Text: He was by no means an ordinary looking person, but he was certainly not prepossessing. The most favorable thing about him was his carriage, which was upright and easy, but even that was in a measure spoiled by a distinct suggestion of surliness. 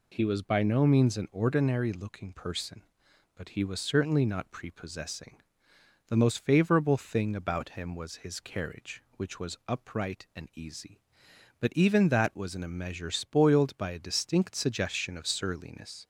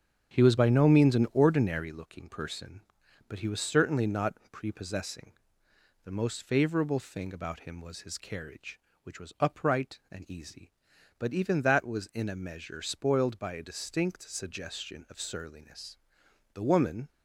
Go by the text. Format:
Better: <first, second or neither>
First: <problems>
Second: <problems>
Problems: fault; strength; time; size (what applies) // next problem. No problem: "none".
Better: first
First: none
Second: starts louder than the rest; strong; until 1.3 s; 8 dB // pauses between "not" and "prepossessing"; slight; at 4.3 s; 0.16 s long // goes on to say "The woman"; from 16.5 s on; 0.56 s long